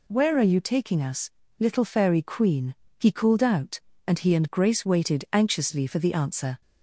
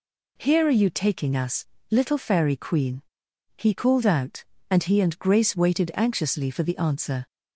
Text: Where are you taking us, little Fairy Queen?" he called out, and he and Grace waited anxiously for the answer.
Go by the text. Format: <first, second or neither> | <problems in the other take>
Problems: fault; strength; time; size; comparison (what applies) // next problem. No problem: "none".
first | says "Here" for "Where"; at 0.3 s